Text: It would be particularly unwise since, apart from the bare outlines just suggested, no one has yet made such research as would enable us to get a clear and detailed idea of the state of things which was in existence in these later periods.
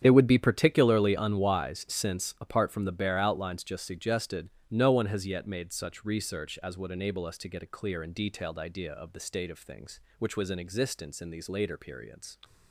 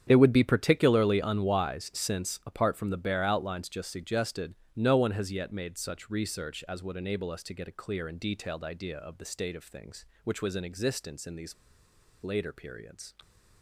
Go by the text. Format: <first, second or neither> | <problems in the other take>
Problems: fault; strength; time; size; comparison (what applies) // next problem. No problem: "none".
first | starts louder than the rest; strong; until 1.0 s; 9 dB; strong in the first // pauses between "these" and "later"; noticeable; at 11.5 s; 0.68 s long